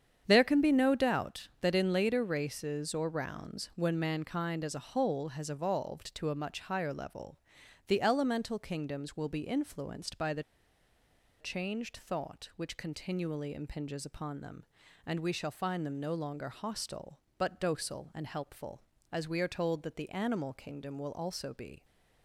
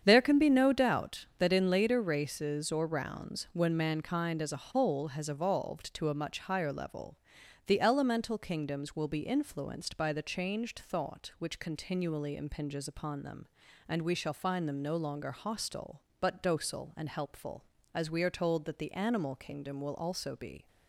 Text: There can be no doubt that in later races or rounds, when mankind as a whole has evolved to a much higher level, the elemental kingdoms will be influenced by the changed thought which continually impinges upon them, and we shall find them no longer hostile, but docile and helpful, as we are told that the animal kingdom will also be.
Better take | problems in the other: second | starts louder than the rest; strong; until 1.2 s; 8 dB; strong in the second // pauses between "the" and "changed"; at 10.4 s; 0.98 s long

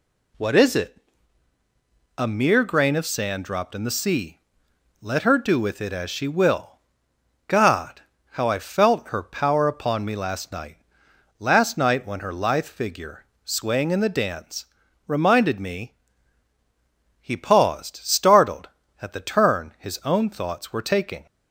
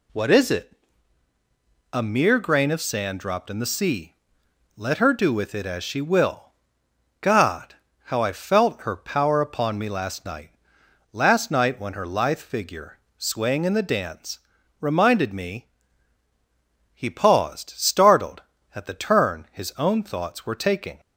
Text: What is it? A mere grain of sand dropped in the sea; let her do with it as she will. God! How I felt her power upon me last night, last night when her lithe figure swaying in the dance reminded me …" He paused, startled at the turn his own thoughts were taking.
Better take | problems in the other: neither | pauses between "figure" and "swaying"; slight; the same in both // pauses between "dance" and "reminded"; the same in both

